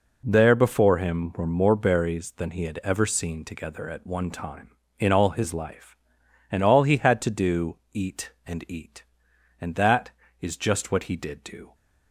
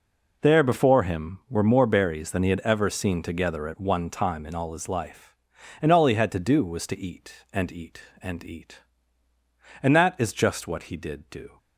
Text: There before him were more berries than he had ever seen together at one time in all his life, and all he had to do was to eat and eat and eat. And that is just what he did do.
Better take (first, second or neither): second